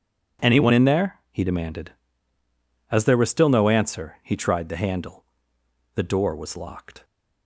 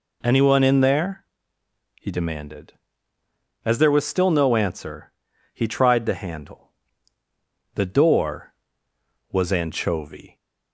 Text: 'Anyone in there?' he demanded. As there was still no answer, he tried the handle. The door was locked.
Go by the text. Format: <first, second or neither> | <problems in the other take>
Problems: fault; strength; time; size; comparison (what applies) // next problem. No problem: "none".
first | says "anchovy" for "locked"; at 9.5 s